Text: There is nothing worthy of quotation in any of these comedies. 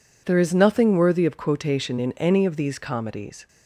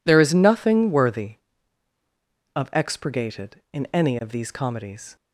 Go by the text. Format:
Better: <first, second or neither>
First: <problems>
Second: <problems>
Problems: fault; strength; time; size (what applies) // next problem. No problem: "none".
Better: first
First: none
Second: says "expurgated" for "quotation"; at 2.7 s